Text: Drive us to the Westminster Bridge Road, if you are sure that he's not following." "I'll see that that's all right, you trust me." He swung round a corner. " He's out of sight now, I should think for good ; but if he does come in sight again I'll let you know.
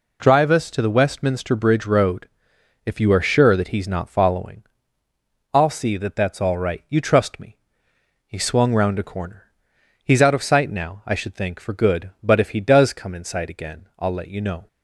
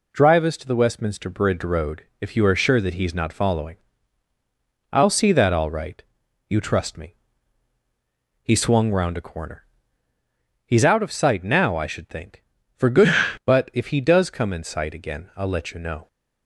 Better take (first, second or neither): first